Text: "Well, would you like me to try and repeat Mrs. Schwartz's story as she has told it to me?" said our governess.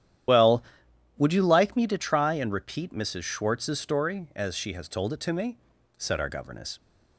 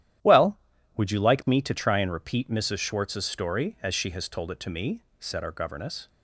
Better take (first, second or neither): second